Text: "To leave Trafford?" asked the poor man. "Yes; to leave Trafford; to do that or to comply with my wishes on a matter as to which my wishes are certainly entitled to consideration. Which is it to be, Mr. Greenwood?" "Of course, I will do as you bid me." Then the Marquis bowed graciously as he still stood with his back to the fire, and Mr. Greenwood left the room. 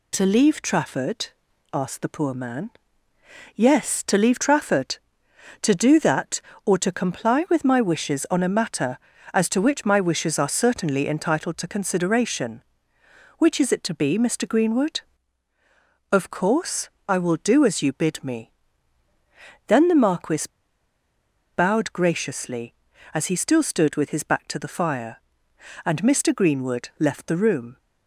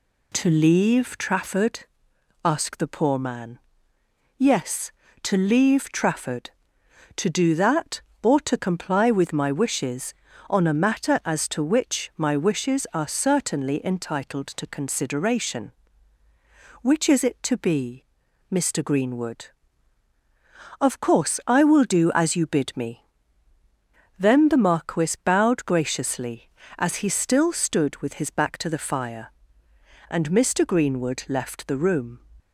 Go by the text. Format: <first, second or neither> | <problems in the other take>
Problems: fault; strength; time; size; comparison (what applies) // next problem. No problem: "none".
second | pauses between "Marquis" and "bowed"; at 20.4 s; 1.0 s long